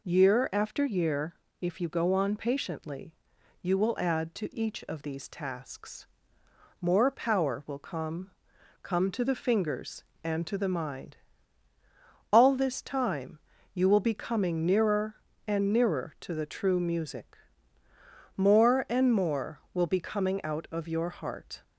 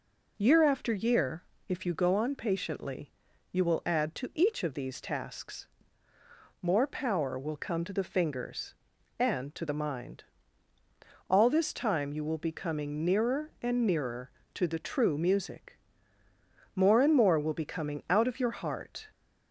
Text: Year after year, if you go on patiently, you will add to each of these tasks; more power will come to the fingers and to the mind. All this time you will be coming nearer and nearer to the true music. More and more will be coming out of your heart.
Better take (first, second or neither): second